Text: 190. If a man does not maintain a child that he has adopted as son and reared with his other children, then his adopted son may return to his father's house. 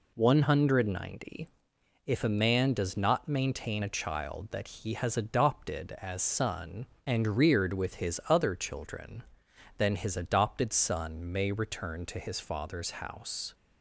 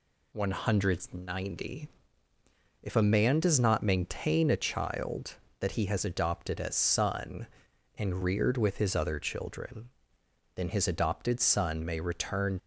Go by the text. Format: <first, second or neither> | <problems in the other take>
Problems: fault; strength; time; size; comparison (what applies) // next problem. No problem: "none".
first | stops before "to his father's house"; at 12.5 s